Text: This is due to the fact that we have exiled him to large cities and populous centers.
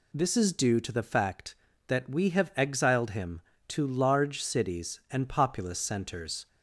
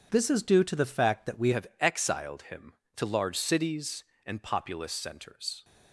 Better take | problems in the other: first | changes voice at "have"; from 1.5 s on; 4.1 s long

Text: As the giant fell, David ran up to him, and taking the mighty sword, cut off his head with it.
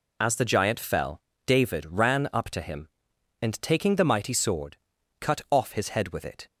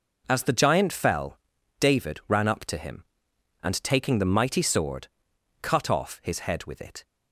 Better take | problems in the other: neither | none

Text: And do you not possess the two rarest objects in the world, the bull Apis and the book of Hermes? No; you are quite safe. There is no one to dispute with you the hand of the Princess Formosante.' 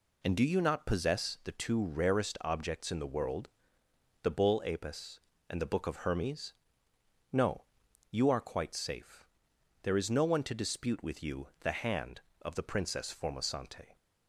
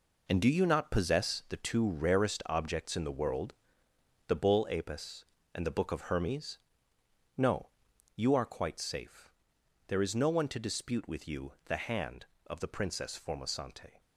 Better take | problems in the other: first | gets quieter; strong; throughout; 9 dB

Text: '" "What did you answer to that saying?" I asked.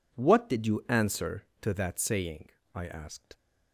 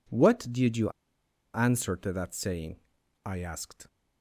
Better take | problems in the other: first | pauses between "you" and "answer"; noticeable; at 0.8 s; 0.64 s long

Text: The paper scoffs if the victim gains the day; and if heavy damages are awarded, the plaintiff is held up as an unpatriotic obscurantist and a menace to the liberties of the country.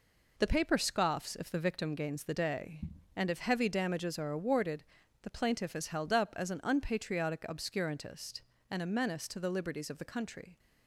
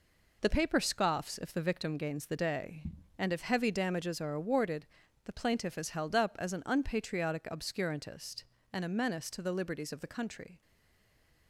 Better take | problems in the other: first | stays silent after the last word; slight; from 10.6 s on; 0.8 s long

